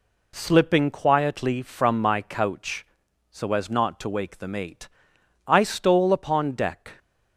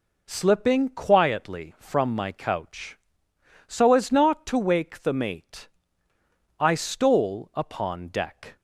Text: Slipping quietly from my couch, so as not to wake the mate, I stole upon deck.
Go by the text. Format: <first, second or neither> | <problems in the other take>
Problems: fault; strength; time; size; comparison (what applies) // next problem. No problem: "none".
neither | none